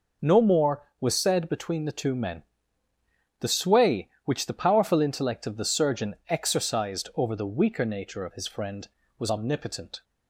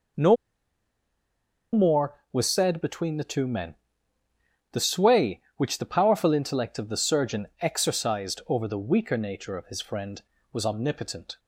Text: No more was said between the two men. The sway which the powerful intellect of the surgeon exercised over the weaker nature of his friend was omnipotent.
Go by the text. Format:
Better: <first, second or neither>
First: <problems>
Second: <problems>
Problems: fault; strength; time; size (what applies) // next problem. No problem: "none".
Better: first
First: none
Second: pauses between "No" and "more"; strong; at 0.3 s; 1.3 s long